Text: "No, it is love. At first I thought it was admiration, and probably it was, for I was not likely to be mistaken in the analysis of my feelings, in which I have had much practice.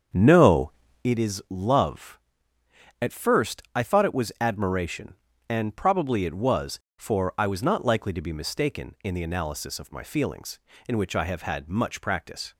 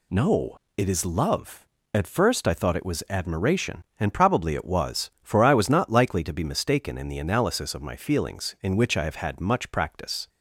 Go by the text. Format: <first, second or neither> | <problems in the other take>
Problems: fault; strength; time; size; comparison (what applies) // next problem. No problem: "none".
second | starts louder than the rest; strong; until 1.1 s; 7.5 dB